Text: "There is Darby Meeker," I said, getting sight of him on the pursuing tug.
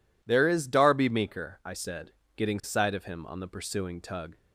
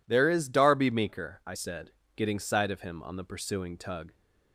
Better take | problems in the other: neither | none

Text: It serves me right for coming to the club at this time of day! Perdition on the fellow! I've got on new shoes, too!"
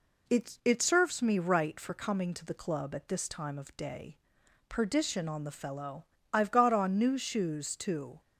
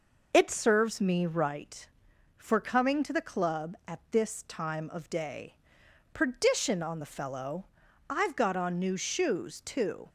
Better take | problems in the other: second | says "It" twice; at 0.6 s

